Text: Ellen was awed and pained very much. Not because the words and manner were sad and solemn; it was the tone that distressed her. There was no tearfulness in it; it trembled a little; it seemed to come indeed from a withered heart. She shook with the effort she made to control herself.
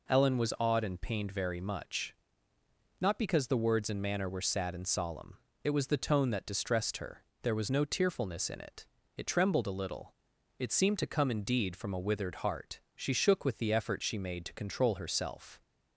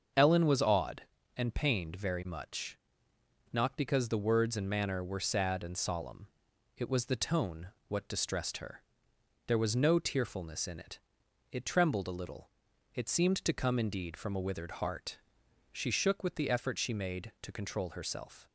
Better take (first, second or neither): first